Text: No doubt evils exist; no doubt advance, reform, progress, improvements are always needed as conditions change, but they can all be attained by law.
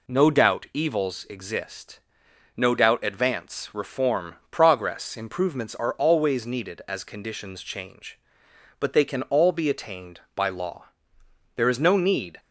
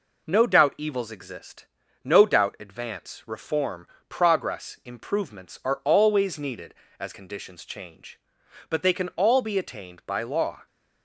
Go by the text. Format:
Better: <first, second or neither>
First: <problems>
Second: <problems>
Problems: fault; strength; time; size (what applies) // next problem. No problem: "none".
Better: second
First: goes on to say "There is no need"; noticeable; from 11.5 s on; 0.84 s long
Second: none